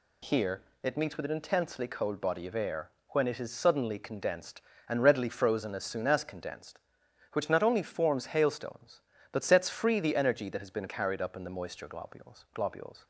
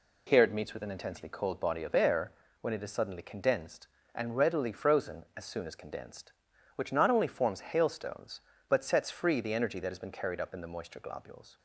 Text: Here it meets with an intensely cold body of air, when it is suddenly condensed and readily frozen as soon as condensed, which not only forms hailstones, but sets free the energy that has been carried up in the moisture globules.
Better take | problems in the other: second | pauses between "Here" and "it"; slight; at 0.6 s; 0.22 s long // says "globules" twice; at 12.5 s

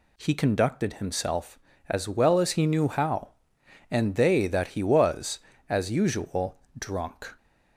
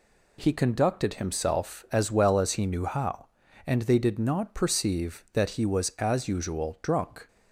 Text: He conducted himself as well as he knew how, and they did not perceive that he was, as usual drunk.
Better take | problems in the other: second | skips "did not perceive"; at 4.4 s // pauses between "usual" and "drunk"; slight; at 6.5 s; 0.20 s long

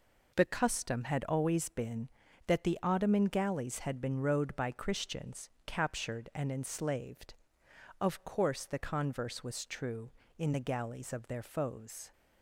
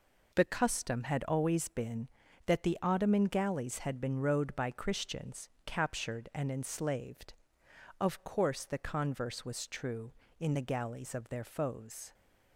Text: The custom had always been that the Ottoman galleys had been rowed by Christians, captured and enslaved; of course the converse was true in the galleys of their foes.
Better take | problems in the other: neither | none

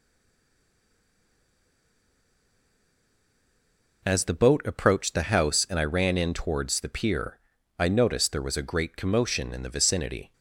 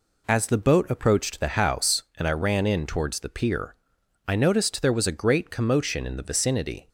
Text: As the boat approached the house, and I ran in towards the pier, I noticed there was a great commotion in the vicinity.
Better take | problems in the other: second | stays silent before the first word; strong; until 4.0 s; 4.0 s long

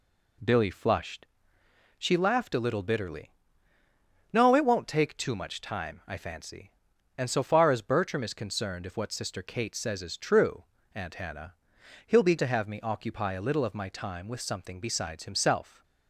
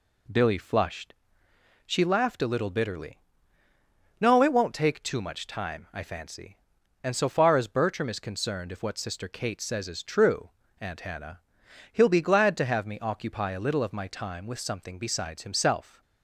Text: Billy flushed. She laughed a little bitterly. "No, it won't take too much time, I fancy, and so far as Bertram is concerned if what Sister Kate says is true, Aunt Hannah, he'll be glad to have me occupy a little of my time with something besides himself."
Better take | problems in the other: second | skips "glad"; at 12.3 s

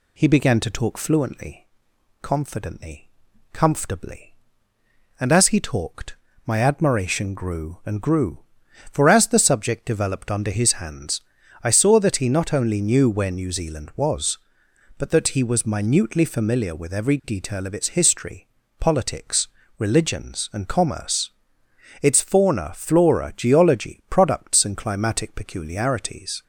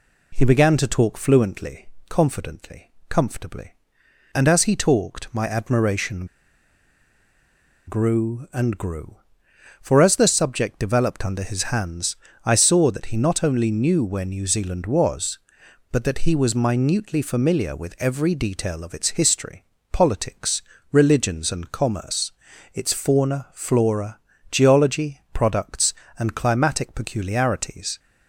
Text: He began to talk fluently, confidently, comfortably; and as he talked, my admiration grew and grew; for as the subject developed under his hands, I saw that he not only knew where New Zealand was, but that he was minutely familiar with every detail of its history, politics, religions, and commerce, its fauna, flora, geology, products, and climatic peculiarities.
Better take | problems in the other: first | pauses between "admiration" and "grew"; strong; at 6.2 s; 1.5 s long

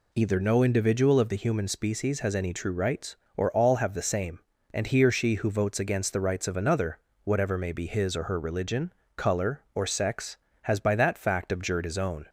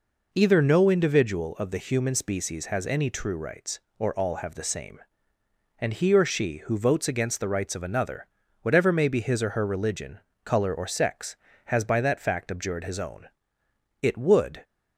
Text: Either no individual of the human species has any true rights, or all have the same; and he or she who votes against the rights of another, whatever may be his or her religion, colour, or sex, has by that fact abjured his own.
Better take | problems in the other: first | goes on to say "It would"; noticeable; from 14.0 s on; 0.62 s long

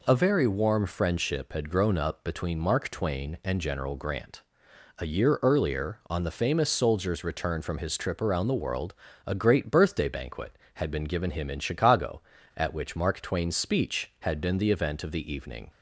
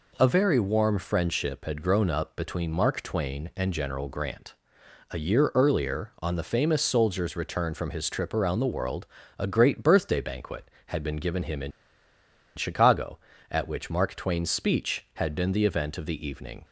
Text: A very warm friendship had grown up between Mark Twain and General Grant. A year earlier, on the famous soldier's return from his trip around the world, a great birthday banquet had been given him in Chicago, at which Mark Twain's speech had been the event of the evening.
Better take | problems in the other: first | pauses between "in" and "Chicago"; noticeable; at 11.7 s; 0.85 s long

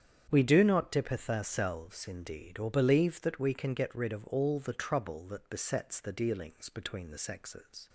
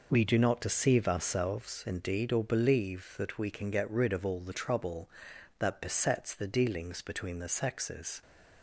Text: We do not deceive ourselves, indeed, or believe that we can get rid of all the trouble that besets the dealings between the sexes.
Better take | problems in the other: second | starts louder than the rest; strong; until 1.3 s; 8.5 dB // says "dippeth" for "deceive"; at 0.9 s

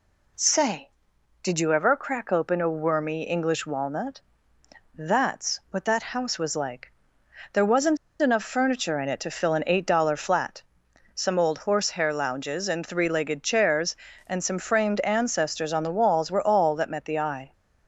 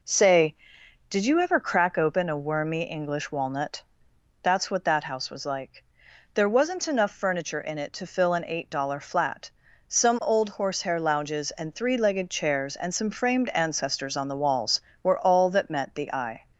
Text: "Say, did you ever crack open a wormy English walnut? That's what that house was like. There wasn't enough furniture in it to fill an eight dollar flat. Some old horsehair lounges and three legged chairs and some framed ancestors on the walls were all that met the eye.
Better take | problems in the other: second | pauses between "wasn't" and "enough"; slight; at 7.9 s; 0.24 s long

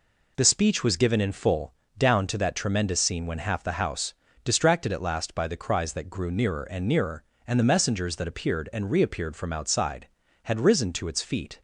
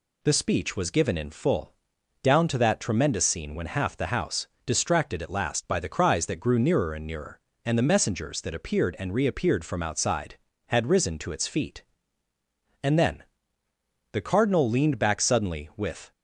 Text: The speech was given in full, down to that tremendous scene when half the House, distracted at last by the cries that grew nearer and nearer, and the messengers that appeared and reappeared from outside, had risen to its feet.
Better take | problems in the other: first | goes on to say "And then The Cardinal leaned back suddenly with"; strong; from 12.8 s on; 3.2 s long

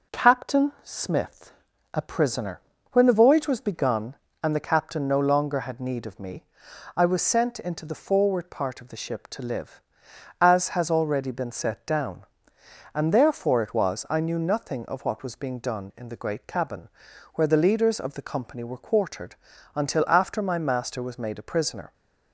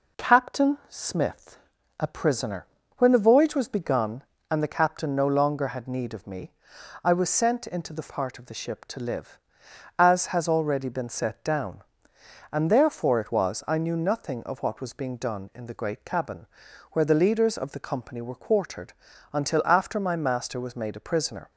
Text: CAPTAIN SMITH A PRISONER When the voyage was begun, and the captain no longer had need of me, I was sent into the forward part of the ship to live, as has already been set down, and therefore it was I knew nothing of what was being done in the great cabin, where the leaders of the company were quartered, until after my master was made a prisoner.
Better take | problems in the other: first | pauses between "SMITH" and "A"; at 1.5 s; 0.42 s long; also in the first // pauses between "PRISONER" and "When"; slight; at 2.6 s; 0.30 s long; slight in the first // skips "forward"; at 8.0 s

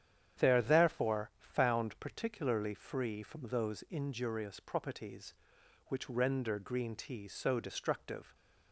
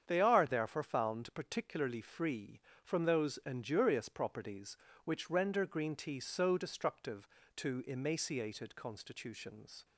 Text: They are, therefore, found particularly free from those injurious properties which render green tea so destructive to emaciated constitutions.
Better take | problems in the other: second | starts louder than the rest; strong; until 1.4 s; 9 dB; strong in the second // stops before "to emaciated constitutions"; at 8.3 s

